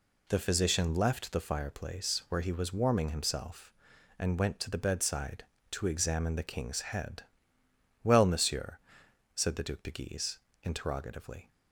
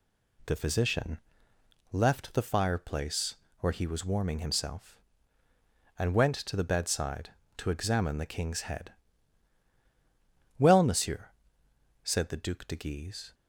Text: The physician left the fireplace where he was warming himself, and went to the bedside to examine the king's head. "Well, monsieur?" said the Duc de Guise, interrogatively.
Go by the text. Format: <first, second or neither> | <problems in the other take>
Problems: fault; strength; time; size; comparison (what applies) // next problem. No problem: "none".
first | pauses between "physician" and "left"; noticeable; at 1.1 s; 0.72 s long // pauses between "fireplace" and "where"; slight; at 3.3 s; 0.24 s long // stops before "interrogatively"; at 13.3 s